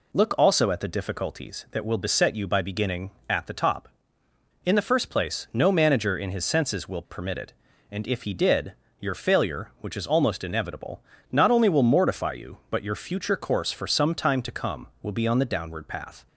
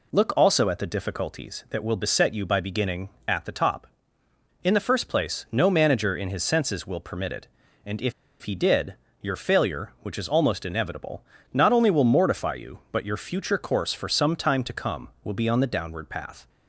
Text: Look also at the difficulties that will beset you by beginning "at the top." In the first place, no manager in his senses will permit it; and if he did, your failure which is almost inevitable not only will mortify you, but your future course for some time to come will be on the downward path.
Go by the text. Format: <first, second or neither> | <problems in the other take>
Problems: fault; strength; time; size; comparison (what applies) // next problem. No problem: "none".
first | pauses between "if" and "he"; slight; at 8.1 s; 0.29 s long // pauses between "inevitable" and "not"; slight; at 11.2 s; 0.30 s long; slight in the first